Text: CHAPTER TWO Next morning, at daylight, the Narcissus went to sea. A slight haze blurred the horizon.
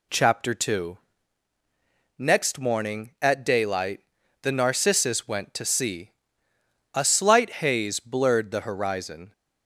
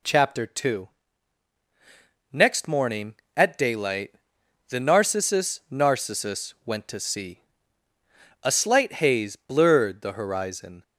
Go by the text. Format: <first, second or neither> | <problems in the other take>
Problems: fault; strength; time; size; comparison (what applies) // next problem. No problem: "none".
first | pauses between "TWO" and "Next"; strong; at 0.8 s; 1.4 s long; also in the first // says "Narcissus" twice; at 5.7 s